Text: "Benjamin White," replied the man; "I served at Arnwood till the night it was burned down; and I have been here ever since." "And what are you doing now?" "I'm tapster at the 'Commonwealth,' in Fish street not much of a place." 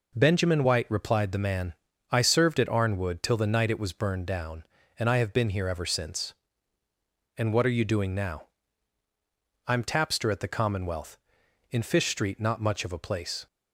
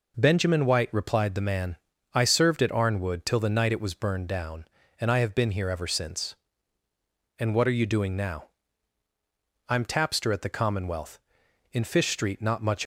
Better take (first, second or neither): first